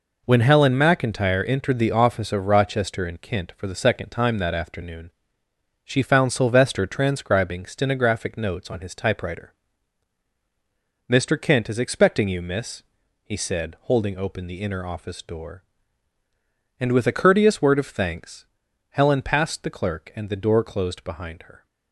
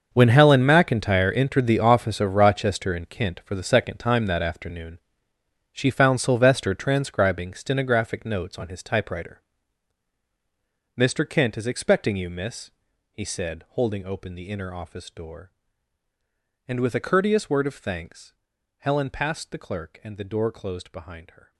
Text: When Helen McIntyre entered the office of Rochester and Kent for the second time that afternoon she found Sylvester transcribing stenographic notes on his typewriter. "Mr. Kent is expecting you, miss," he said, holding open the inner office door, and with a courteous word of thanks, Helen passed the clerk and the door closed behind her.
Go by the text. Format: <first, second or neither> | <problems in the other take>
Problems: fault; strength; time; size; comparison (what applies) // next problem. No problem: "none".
first | gets quieter; strong; throughout; 15.5 dB // pauses between "afternoon" and "she"; noticeable; at 4.9 s; 0.74 s long; noticeable in the first